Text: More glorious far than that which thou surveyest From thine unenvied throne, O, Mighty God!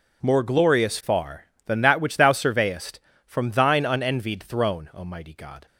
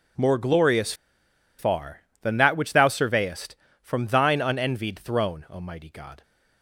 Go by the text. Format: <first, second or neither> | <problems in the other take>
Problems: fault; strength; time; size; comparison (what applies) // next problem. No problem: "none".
first | pauses between "glorious" and "far"; noticeable; at 0.9 s; 0.65 s long